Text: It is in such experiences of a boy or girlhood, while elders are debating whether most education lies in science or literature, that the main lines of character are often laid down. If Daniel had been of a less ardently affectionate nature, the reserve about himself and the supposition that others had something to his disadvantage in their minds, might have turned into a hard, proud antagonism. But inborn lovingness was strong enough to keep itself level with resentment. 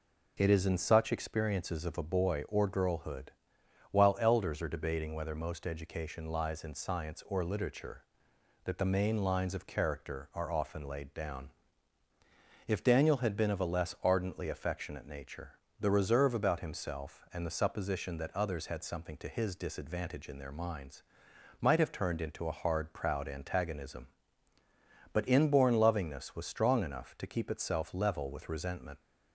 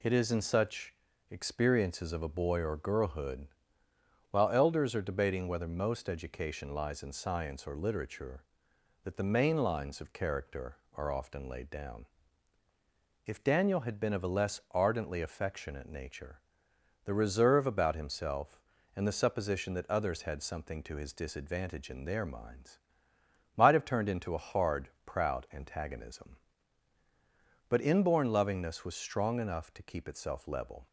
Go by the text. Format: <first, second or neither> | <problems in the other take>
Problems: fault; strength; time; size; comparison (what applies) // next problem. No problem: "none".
first | pauses between "such" and "experiences"; slight; at 0.9 s; 0.34 s long // stops before "with resentment"; at 30.8 s